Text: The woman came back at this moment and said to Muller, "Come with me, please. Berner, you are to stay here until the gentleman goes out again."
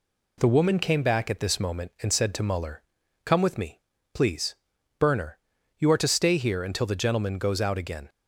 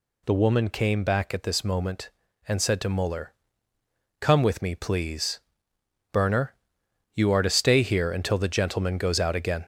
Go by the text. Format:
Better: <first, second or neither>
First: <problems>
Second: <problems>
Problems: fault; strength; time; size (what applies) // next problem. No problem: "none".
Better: first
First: none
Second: gets louder; noticeable; throughout; 4 dB